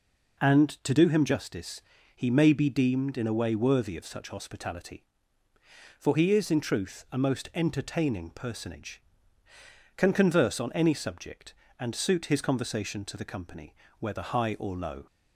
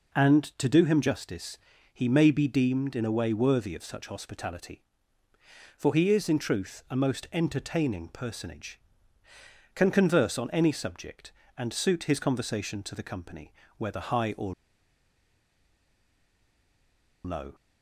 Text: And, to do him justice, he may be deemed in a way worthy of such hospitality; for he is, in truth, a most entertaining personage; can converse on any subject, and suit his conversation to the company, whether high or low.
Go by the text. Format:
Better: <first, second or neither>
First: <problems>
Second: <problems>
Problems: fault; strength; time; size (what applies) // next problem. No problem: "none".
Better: first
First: none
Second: pauses between "or" and "low"; strong; at 14.5 s; 2.7 s long